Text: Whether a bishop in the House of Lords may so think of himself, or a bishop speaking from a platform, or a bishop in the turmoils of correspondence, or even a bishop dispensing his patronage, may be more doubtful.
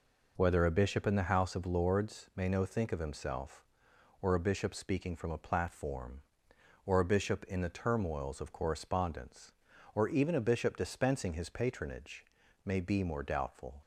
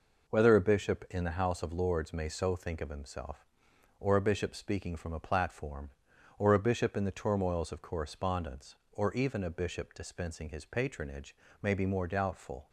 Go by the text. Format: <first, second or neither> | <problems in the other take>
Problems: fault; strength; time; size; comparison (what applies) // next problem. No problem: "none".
second | says "no" for "so"; at 2.4 s